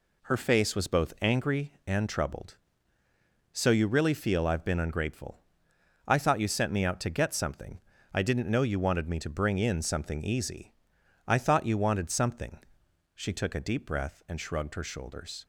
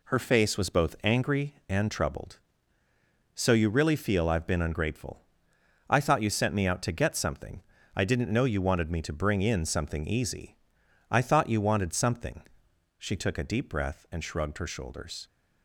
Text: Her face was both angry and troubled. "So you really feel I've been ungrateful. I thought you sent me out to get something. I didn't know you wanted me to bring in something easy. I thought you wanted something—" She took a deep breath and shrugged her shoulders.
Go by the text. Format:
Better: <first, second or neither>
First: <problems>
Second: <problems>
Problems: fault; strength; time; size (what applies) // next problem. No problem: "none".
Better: neither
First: none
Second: none